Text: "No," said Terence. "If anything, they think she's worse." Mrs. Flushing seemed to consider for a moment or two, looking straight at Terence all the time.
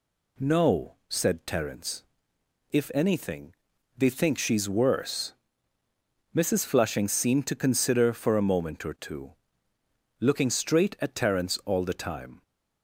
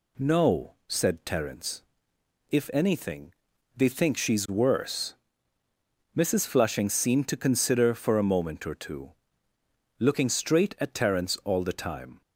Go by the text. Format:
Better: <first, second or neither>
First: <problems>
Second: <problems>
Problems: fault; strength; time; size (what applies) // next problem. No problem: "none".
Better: neither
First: none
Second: none